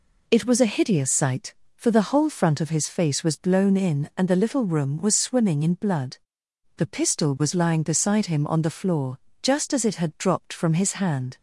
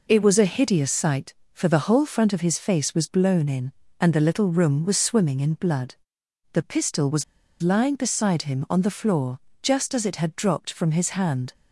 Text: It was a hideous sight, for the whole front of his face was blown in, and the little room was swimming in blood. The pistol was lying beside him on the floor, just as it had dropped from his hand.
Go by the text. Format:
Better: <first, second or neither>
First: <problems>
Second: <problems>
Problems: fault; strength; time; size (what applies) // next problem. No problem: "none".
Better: first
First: none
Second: pauses between "was" and "lying"; at 7.2 s; 0.39 s long